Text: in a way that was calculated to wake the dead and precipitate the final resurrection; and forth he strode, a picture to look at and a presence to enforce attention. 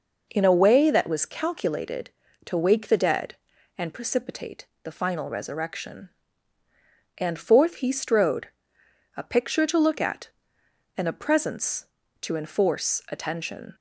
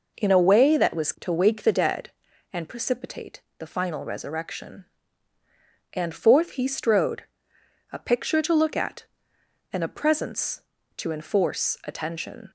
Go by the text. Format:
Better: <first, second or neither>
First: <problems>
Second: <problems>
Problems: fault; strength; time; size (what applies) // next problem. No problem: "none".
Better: first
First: pauses between "precipitate" and "the"; slight; at 4.6 s; 0.18 s long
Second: skips "calculated"; at 1.1 s // pauses between "precipitate" and "the"; slight; at 3.4 s; 0.18 s long